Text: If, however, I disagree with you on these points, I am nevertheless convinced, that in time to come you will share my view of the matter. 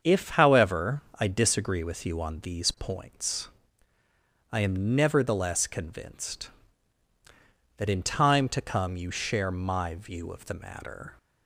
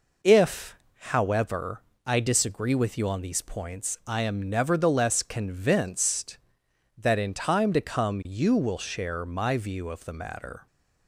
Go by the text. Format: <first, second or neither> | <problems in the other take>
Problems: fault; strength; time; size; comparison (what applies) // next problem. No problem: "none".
second | starts louder than the rest; until 1.2 s; 7 dB // skips "will"; at 9.1 s